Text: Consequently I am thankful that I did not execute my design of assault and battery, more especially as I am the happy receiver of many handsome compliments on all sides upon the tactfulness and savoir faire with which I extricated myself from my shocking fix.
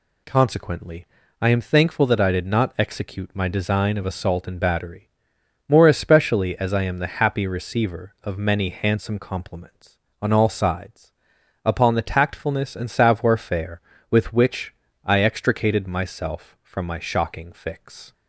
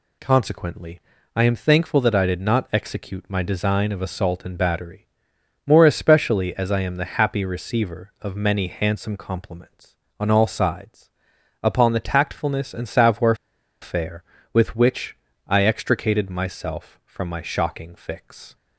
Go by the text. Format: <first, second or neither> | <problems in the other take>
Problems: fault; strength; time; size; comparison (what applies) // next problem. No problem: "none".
first | pauses between "Consequently" and "I"; slight; at 1.0 s; 0.34 s long; slight in the first // pauses between "sides" and "upon"; noticeable; at 11.1 s; 0.52 s long; noticeable in the first // pauses between "savoir" and "faire"; noticeable; at 13.3 s; 0.47 s long // pauses between "which" and "I"; slight; at 15.1 s; 0.32 s long; slight in the first